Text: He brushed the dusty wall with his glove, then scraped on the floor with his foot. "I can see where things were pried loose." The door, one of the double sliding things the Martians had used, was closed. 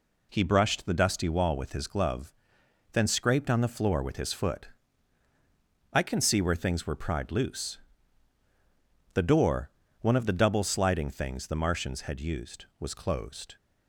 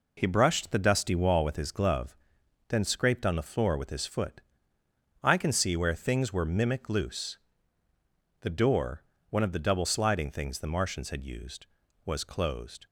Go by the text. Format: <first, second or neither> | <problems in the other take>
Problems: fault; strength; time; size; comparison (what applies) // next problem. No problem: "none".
first | says "mimic" for "pried"; at 6.4 s